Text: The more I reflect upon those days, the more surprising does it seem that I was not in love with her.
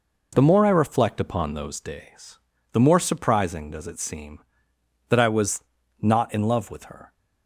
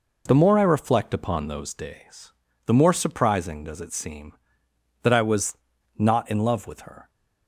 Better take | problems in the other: neither | pauses between "was" and "not"; the same in both

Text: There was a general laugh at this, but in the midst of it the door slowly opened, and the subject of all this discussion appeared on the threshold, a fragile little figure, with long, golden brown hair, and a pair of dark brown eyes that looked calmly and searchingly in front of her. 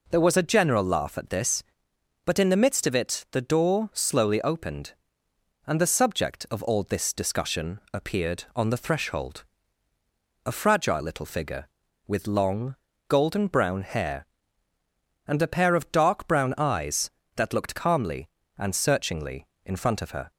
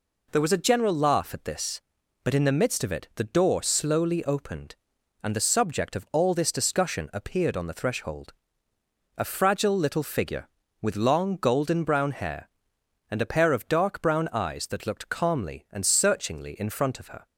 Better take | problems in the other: neither | none

